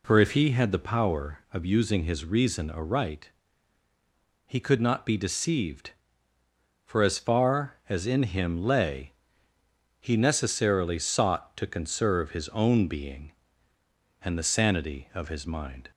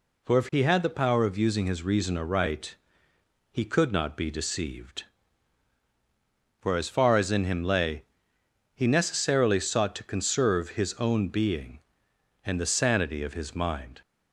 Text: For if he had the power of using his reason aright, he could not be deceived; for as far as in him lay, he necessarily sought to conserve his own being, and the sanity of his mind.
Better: neither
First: none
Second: none

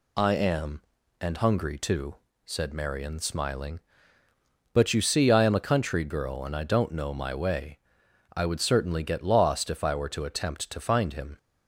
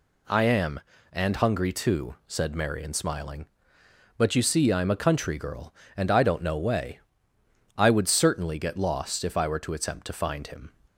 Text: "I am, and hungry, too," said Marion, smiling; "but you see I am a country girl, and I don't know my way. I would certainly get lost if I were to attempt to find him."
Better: first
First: none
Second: skips "my"; at 6.5 s

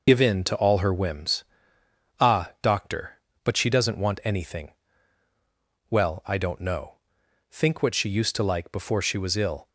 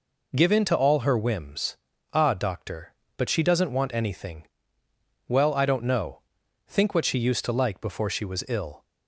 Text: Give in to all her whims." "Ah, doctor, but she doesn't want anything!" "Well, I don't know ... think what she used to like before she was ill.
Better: second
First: loses the start of "Give"; at 0.0 s; 45 ms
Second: none

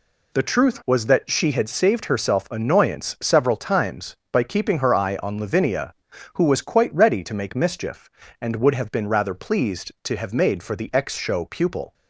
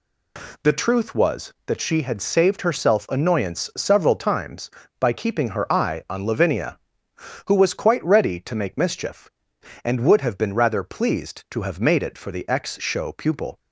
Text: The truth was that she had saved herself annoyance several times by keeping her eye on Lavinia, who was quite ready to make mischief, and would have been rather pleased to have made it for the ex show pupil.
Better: second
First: skips "it"; at 10.6 s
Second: none

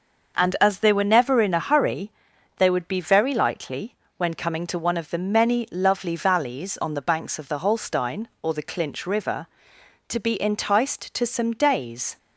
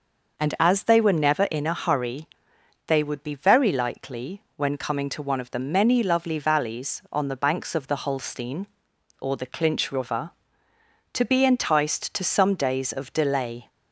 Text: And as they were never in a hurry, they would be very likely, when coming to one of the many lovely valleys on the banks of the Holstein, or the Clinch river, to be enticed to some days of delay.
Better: second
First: starts louder than the rest; noticeable; until 1.4 s; 6 dB // stops before "of delay"; at 12.1 s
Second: none

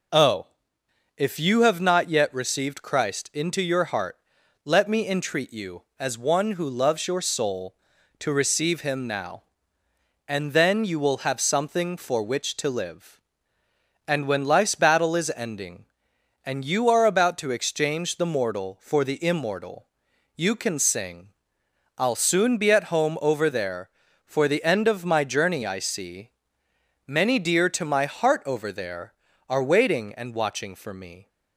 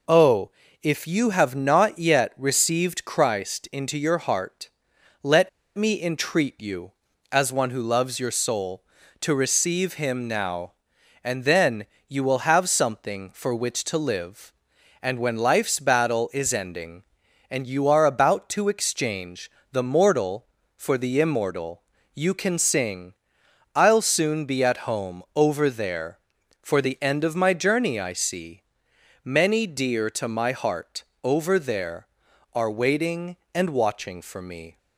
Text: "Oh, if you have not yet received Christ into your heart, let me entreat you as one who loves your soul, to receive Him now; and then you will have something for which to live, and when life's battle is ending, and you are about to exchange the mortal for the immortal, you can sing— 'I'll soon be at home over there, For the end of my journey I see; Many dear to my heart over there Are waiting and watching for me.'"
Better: first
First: none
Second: pauses between "let" and "me"; slight; at 5.4 s; 0.26 s long // pauses between "then" and "you"; slight; at 11.8 s; 0.22 s long // pauses between "exchange" and "the"; slight; at 19.5 s; 0.20 s long // pauses between "heart" and "over"; slight; at 31.0 s; 0.20 s long

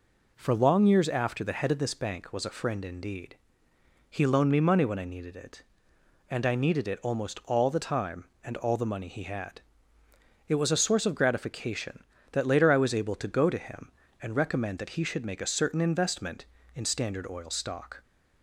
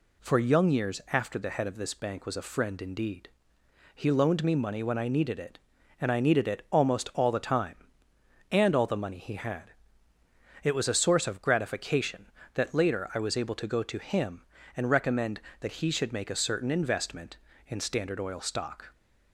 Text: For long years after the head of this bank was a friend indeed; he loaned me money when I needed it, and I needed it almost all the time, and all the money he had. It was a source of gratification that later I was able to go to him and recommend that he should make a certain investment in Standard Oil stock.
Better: first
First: none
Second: says "young" for "long"; at 0.3 s

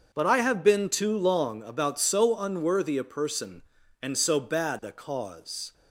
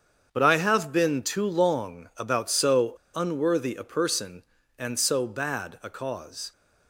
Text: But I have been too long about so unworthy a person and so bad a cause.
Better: first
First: starts louder than the rest; until 1.1 s; 6 dB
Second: starts louder than the rest; strong; until 1.3 s; 7.5 dB // pauses between "so" and "unworthy"; slight; at 2.9 s; 0.20 s long

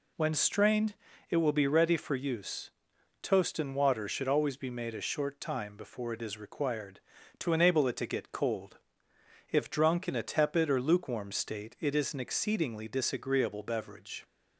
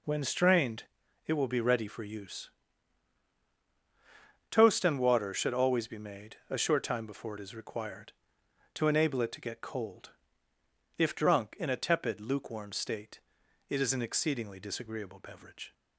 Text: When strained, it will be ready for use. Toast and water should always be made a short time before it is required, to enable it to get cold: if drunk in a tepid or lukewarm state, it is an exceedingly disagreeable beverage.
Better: first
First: none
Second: skips "or"; at 12.1 s

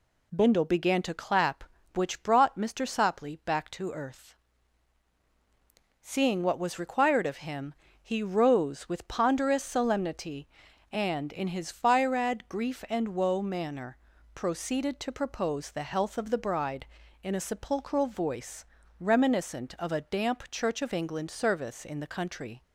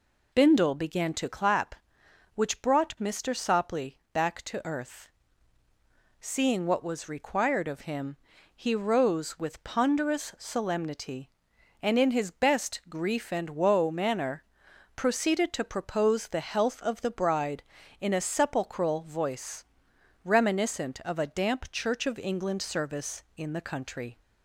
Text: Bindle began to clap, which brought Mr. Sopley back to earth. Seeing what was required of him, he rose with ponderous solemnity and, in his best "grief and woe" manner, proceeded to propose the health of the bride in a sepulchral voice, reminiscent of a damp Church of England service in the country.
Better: second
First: says "firad" for "best"; at 11.7 s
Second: none

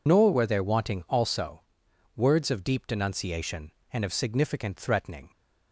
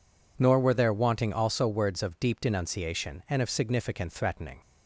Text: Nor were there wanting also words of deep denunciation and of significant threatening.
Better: second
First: loses the start of "Nor"; at 0.0 s; 55 ms // pauses between "also" and "words"; noticeable; at 1.6 s; 0.52 s long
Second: none

